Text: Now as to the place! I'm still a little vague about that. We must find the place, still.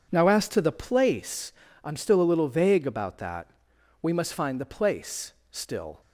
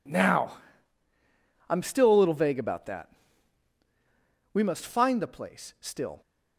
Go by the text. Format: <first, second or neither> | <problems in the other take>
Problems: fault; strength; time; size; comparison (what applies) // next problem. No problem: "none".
first | skips "as to the place"; at 1.1 s